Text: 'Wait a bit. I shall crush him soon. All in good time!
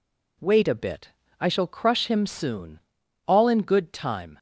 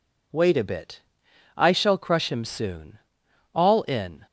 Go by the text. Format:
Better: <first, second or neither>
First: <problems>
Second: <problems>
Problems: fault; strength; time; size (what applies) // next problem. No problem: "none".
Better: first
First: none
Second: stops before "good time"; at 4.2 s